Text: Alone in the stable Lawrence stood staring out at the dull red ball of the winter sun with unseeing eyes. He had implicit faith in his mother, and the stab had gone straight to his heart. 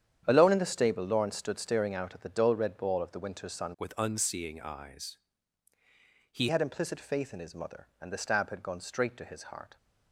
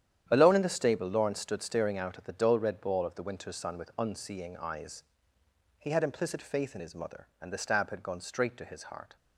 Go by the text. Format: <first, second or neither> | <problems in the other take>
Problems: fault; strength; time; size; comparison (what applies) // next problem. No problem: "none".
second | starts louder than the rest; strong; until 1.2 s; 9 dB; strong in the second // changes voice from "with" to "He"; from 3.7 to 6.4 s; 2.7 s long